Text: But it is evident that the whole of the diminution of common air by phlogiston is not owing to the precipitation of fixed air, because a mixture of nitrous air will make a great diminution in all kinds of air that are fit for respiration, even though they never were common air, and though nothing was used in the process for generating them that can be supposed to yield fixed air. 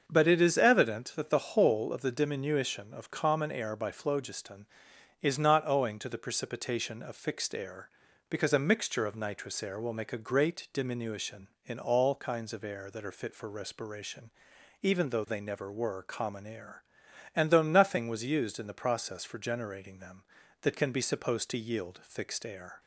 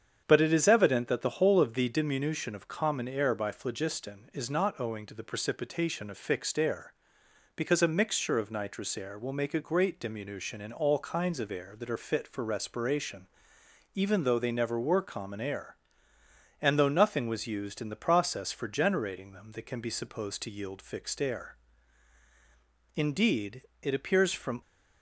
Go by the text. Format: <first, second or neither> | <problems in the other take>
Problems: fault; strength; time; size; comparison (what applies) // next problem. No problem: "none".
first | starts louder than the rest; strong; until 1.2 s; 8 dB; also in the first // goes on to say "Indeed it appears from"; strong; from 22.9 s on; 1.6 s long